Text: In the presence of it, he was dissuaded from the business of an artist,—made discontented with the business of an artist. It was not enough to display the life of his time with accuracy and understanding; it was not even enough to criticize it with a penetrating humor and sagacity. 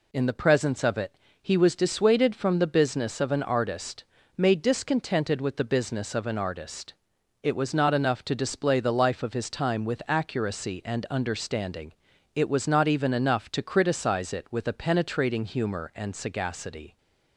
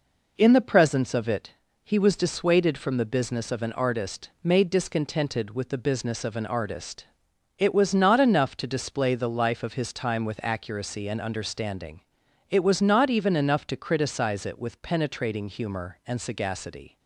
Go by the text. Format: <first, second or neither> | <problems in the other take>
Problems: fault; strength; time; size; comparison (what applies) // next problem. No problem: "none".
first | skips "a"; at 14.8 s